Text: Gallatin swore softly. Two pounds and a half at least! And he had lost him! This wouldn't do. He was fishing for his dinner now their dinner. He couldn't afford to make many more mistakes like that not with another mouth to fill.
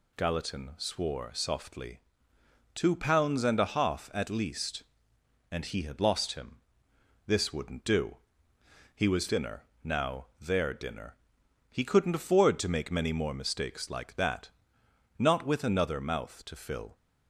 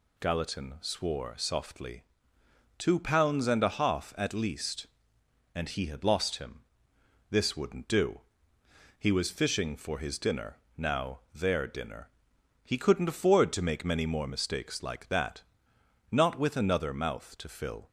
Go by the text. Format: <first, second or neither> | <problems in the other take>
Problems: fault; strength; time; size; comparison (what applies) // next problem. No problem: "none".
second | skips "fishing for his"; at 9.2 s // pauses between "dinner" and "now"; slight; at 9.6 s; 0.22 s long; slight in the second // pauses between "that" and "not"; noticeable; at 14.4 s; 0.70 s long; noticeable in the second